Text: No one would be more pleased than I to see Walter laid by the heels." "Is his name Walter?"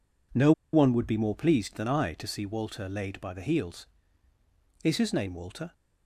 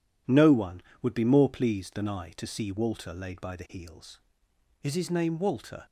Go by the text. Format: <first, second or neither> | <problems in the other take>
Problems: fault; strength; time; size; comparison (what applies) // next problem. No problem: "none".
second | pauses between "No" and "one"; slight; at 0.5 s; 0.21 s long